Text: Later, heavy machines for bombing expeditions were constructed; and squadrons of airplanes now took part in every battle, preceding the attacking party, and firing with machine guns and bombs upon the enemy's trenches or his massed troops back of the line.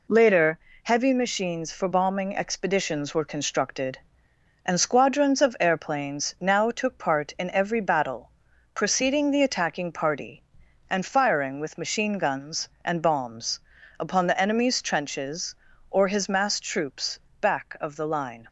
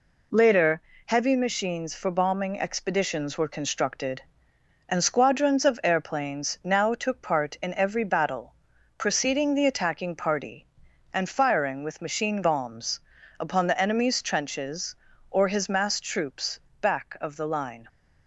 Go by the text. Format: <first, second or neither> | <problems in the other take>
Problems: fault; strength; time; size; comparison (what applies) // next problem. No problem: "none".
first | skips "guns and"; at 12.4 s // pauses between "bombs" and "upon"; at 12.9 s; 0.40 s long; also in the first // pauses between "troops" and "back"; slight; at 16.5 s; 0.22 s long; slight in the first